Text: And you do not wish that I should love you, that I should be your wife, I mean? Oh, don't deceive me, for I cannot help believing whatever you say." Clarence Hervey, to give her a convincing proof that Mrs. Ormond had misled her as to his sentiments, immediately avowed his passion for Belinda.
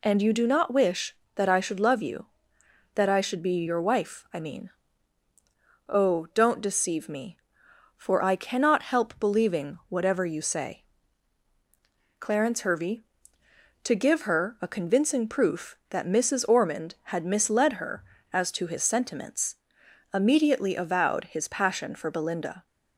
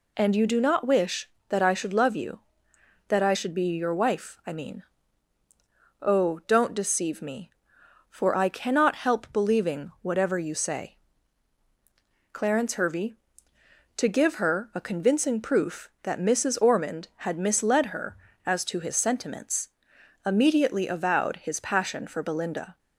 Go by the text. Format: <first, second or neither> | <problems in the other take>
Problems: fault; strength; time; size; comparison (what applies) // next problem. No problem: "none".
neither | none